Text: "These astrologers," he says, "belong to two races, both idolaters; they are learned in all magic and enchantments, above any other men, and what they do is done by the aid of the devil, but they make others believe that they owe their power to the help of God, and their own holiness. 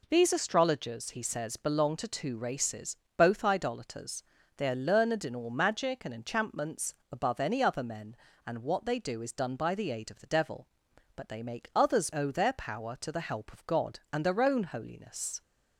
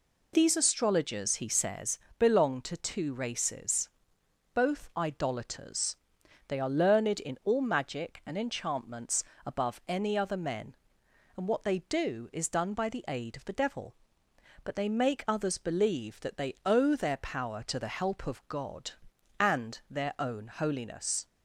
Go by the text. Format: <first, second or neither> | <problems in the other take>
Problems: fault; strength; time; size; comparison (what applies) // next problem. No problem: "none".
second | skips "believe that they"; at 12.1 s